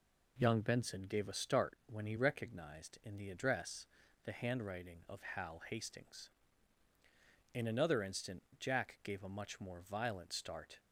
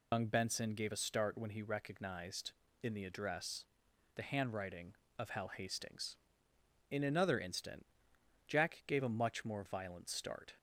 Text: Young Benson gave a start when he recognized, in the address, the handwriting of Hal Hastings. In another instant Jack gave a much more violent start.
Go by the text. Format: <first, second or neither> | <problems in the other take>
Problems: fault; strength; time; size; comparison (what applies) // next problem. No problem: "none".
first | loses the start of "Young"; at 0.1 s; 95 ms // pauses between "instant" and "Jack"; noticeable; at 7.8 s; 0.62 s long; slight in the first